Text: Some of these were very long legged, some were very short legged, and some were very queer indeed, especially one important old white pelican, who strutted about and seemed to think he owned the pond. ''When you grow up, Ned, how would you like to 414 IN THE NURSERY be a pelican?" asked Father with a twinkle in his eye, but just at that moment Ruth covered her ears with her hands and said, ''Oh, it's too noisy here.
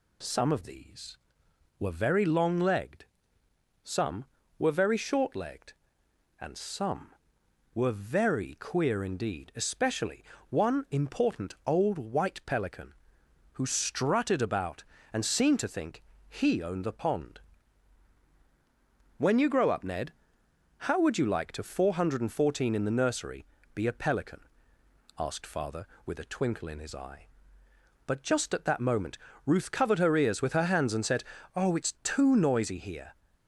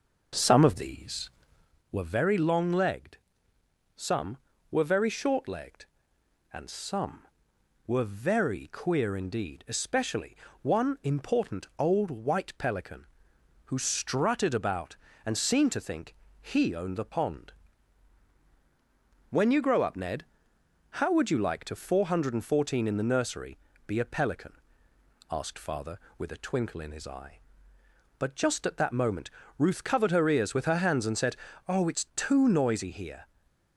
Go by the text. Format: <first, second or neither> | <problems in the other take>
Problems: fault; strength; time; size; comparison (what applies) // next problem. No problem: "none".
first | starts louder than the rest; noticeable; until 1.8 s; 5.5 dB // pauses between "especially" and "one"; slight; at 10.3 s; 0.26 s long; slight in the first // pauses between "think" and "he"; slight; at 16.1 s; 0.26 s long; slight in the first // pauses between "NURSERY" and "be"; slight; at 23.5 s; 0.30 s long; slight in the first // pauses between "moment" and "Ruth"; slight; at 29.2 s; 0.28 s long; slight in the first // stays silent after the last word; slight; from 33.2 s on; 0.5 s long